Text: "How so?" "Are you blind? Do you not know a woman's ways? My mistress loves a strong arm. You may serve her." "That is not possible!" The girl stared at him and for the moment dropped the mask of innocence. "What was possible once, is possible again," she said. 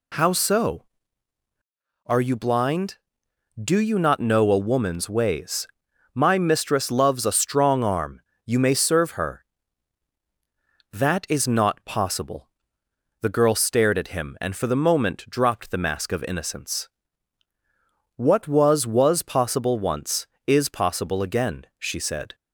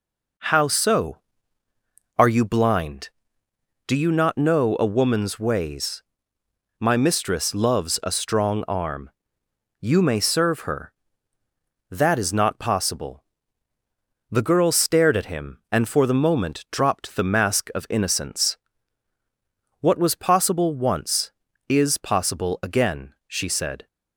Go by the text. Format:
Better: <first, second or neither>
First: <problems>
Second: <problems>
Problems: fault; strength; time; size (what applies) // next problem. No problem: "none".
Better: second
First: says "was" twice; at 18.8 s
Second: none